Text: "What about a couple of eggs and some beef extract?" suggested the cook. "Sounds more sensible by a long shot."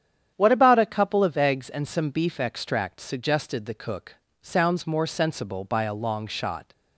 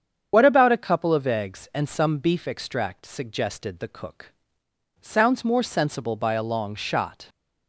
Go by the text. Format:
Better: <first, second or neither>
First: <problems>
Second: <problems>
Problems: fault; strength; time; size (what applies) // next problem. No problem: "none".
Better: first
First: starts louder than the rest; strong; until 1.3 s; 9.5 dB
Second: loses the start of "What"; at 0.3 s; 50 ms // starts louder than the rest; strong; until 1.3 s; 8 dB